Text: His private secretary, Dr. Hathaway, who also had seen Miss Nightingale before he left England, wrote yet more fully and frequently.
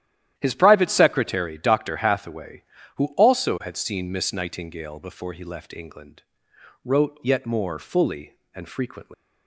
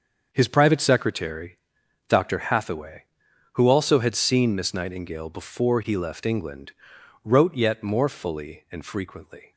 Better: second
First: starts louder than the rest; strong; until 1.3 s; 11.5 dB // leaves "frequently" unfinished; at 9.1 s; 190 ms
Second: starts louder than the rest; until 1.3 s; 6.5 dB

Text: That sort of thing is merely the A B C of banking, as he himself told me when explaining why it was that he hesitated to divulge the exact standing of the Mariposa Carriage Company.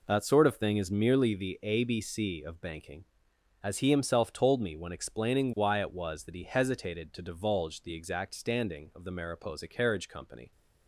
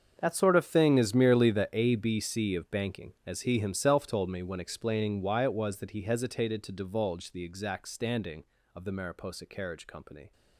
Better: first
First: none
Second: gets quieter; strong; throughout; 16 dB

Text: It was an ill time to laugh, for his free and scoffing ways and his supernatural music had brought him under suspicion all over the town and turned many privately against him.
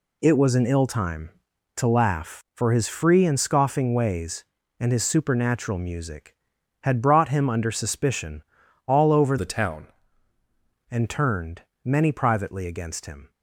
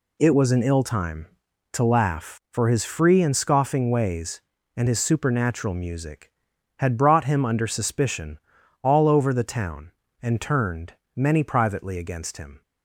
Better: second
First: pauses between "suspicion" and "all"; noticeable; at 8.4 s; 0.46 s long // changes voice from "the" to "town"; from 9.3 to 9.8 s; 0.5 s long // pauses between "turned" and "many"; slight; at 11.6 s; 0.22 s long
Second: pauses between "suspicion" and "all"; noticeable; at 8.3 s; 0.46 s long // pauses between "turned" and "many"; slight; at 10.9 s; 0.22 s long

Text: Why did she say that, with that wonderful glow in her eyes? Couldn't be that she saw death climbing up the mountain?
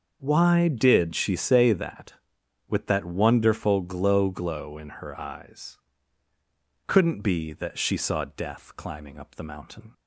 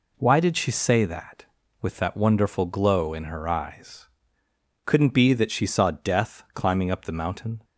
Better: second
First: starts louder than the rest; until 1.2 s; 6.5 dB // says "glow" twice; at 4.2 s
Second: none

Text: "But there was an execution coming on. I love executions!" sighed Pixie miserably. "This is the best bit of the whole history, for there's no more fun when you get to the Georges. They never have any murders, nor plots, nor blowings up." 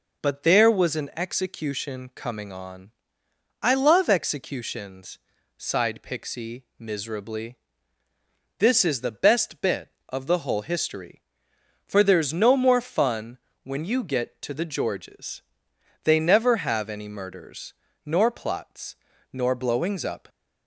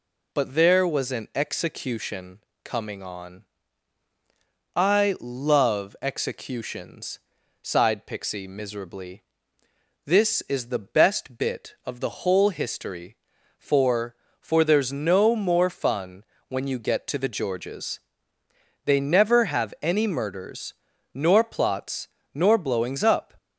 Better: first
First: pauses between "fun" and "when"; slight; at 13.3 s; 0.24 s long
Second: pauses between "execution" and "coming"; slight; at 2.3 s; 0.24 s long // says "for" twice; at 14.3 s // pauses between "fun" and "when"; slight; at 16.2 s; 0.24 s long

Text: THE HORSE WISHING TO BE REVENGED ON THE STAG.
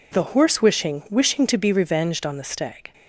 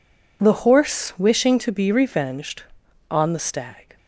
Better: second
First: says "WISHING" twice; at 1.0 s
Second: none

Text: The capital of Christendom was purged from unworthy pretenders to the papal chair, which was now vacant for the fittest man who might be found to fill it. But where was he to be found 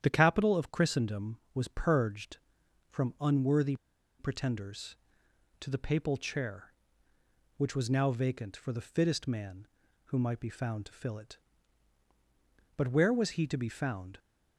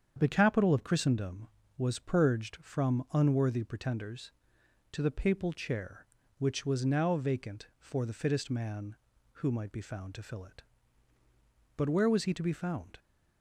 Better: second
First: starts louder than the rest; strong; until 1.0 s; 9.5 dB // pauses between "unworthy" and "pretenders"; at 3.7 s; 0.44 s long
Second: starts louder than the rest; strong; until 1.1 s; 7.5 dB

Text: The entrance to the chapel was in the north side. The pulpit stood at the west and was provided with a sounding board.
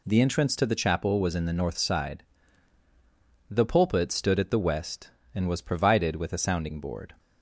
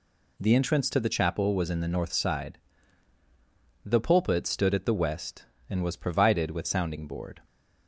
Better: first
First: none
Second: skips "a"; at 6.6 s

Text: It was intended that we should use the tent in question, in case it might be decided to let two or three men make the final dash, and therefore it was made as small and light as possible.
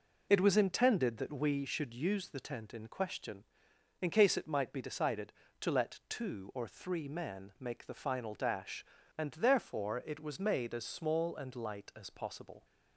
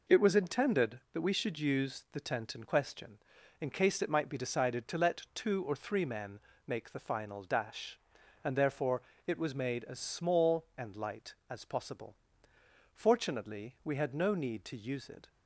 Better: first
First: none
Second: pauses between "men" and "make"; slight; at 6.3 s; 0.26 s long // pauses between "therefore" and "it"; slight; at 9.0 s; 0.24 s long // goes on to say "Fortunately we had no need to use it"; strong; from 12.9 s on; 2.3 s long

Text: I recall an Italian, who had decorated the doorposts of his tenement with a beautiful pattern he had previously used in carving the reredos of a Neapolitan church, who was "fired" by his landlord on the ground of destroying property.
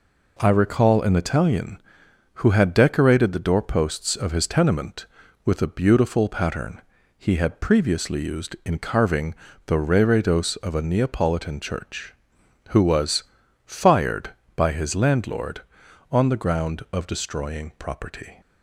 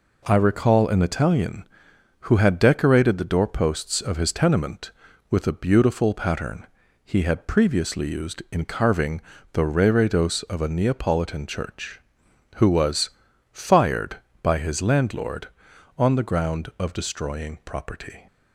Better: neither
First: pauses between "pattern" and "he"; at 6.7 s; 0.36 s long // pauses between "carving" and "the"; slight; at 9.3 s; 0.30 s long // pauses between "was" and "fired"; at 13.2 s; 0.42 s long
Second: pauses between "pattern" and "he"; at 6.6 s; 0.38 s long // pauses between "carving" and "the"; slight; at 9.2 s; 0.30 s long // pauses between "was" and "fired"; at 13.0 s; 0.42 s long

